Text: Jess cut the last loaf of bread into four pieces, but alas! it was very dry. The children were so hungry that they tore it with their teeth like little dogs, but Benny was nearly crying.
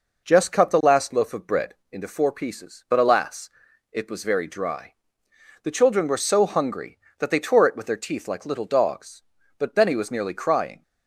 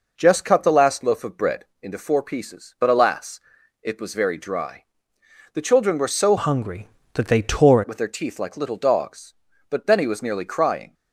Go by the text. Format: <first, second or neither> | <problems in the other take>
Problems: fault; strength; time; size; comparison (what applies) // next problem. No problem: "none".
first | pauses between "bread" and "into"; slight; at 1.6 s; 0.18 s long; slight in the first // changes voice from "hungry" to "tore"; from 6.3 to 7.8 s; 1.5 s long